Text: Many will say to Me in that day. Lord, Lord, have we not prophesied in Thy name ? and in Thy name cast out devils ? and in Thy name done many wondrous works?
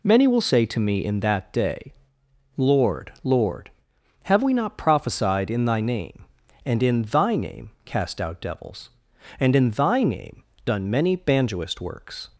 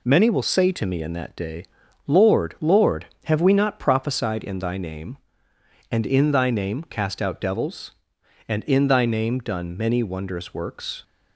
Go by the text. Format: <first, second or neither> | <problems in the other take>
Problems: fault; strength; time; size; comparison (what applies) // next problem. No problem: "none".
second | pauses between "name" and "done"; slight; at 10.4 s; 0.24 s long // says "banjoist" for "wondrous"; at 11.1 s